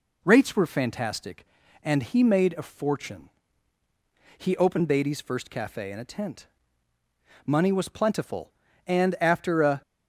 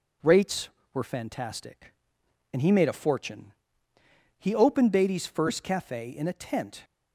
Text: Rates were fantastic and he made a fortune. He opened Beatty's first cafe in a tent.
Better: second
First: goes on to say "Money was plentiful and after a"; strong; from 7.4 s on; 2.3 s long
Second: none

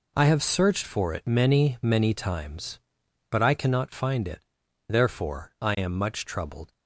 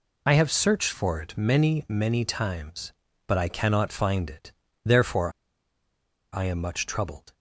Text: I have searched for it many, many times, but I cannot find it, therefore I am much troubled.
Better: first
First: none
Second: pauses between "therefore" and "I"; at 5.3 s; 1.0 s long

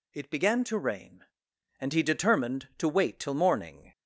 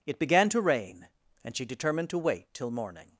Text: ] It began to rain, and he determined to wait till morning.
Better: first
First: none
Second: says "she" for "he"; at 1.5 s

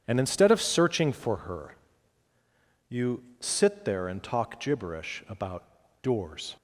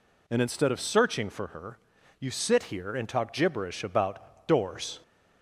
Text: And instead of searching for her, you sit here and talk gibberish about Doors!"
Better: second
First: pauses between "you" and "sit"; slight; at 3.2 s; 0.18 s long // says "there" for "here"; at 3.8 s // pauses between "about" and "Doors"; at 5.6 s; 0.37 s long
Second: none

